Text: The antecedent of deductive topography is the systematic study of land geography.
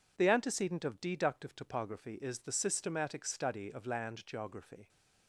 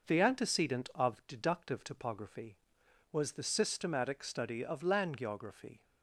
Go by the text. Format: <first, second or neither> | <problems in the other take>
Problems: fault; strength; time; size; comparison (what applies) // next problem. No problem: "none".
first | says "was" for "is"; at 3.0 s